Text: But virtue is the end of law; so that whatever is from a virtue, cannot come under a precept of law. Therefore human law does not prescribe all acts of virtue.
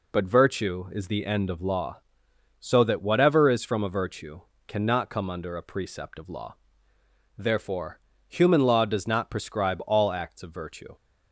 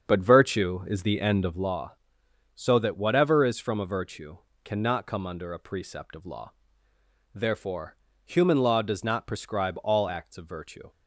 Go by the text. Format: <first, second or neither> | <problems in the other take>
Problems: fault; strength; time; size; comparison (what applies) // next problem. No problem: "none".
first | starts louder than the rest; until 1.6 s; 7 dB // pauses between "Therefore" and "human"; slight; at 7.9 s; 0.28 s long; slight in the first